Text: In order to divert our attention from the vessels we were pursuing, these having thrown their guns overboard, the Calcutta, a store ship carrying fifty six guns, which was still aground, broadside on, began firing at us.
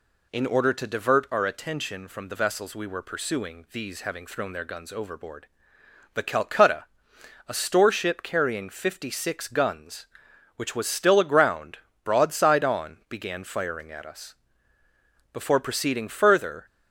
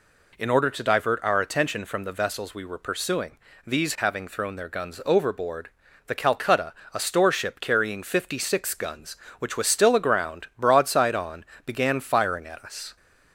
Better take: second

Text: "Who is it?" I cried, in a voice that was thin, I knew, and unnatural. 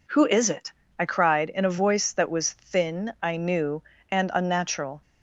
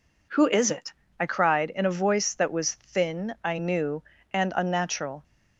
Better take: neither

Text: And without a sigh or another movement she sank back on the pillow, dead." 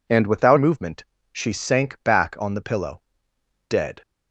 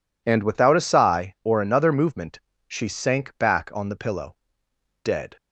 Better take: second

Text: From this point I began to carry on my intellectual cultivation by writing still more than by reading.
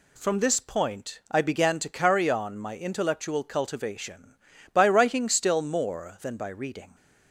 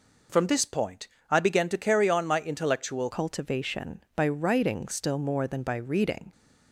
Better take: first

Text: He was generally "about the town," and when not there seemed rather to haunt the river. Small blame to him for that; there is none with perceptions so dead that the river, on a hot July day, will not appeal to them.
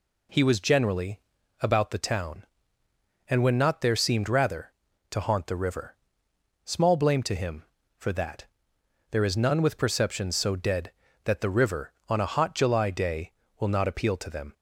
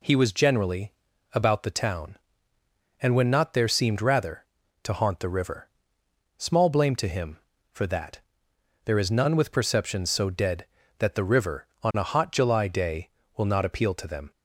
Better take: neither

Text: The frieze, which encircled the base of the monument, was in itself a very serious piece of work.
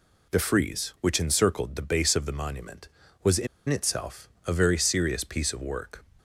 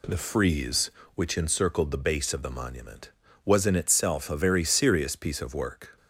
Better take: second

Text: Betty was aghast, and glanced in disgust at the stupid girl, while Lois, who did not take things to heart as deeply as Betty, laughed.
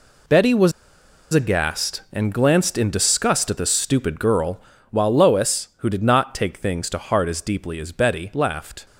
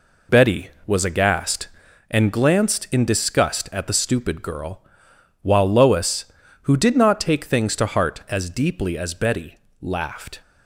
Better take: second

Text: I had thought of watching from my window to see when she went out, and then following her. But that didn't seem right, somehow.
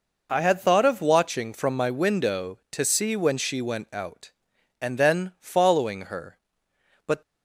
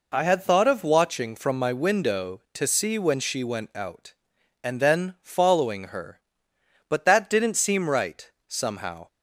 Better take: second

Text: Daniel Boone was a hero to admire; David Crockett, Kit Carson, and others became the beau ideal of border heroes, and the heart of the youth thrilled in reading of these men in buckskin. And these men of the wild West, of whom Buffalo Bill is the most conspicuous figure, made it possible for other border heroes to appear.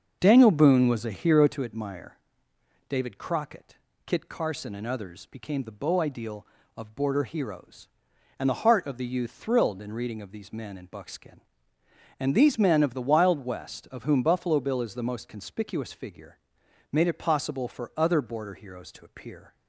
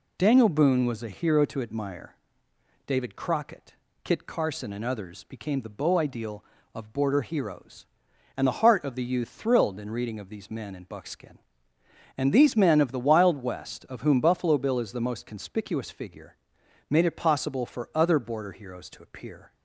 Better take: second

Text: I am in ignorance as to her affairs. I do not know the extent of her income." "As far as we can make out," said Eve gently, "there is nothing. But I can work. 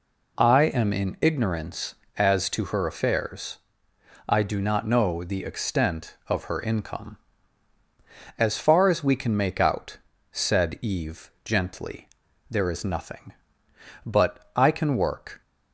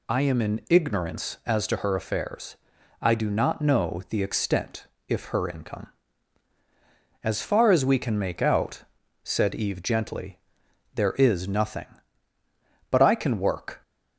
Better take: first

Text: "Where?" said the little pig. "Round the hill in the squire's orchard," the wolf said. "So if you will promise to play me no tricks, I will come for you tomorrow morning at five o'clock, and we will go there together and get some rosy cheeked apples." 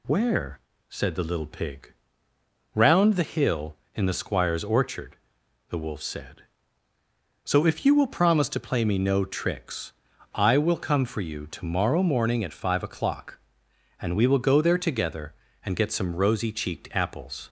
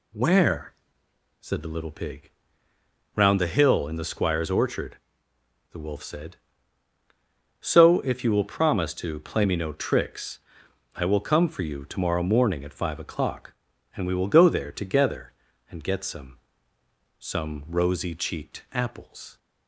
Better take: first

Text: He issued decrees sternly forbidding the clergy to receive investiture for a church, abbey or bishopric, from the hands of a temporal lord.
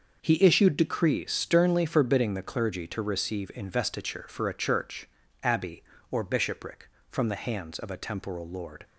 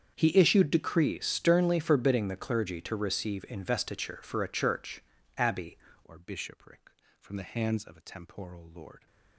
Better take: first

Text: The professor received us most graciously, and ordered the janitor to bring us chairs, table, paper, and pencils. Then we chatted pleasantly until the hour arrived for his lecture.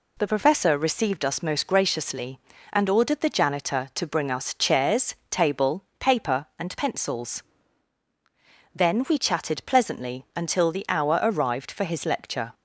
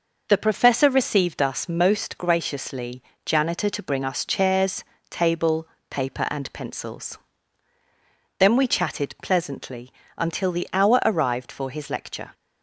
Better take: first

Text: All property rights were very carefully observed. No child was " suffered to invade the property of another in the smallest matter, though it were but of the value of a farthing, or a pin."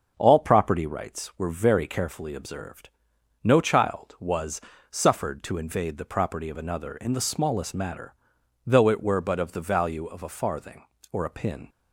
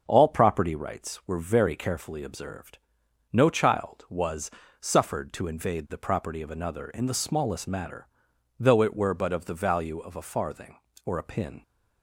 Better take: neither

